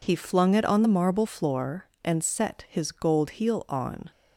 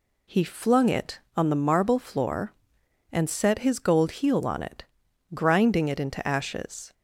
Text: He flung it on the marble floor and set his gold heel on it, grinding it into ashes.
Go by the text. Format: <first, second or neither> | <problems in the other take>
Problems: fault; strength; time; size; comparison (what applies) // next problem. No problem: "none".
second | stops before "it grinding it into ashes"; at 4.1 s